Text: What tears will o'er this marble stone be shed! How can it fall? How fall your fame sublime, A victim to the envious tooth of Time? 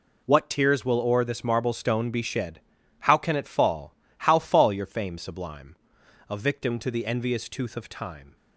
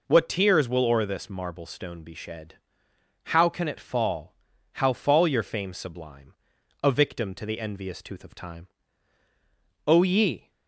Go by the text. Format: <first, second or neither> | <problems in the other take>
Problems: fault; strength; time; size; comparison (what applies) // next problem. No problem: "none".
first | goes on to say "O ye"; noticeable; from 9.8 s on; 0.64 s long